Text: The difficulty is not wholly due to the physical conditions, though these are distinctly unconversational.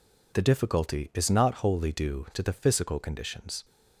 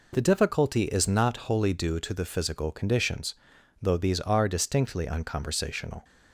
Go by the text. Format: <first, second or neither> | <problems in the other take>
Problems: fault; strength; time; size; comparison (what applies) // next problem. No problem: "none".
second | stops before "though these are distinctly unconversational"; at 3.6 s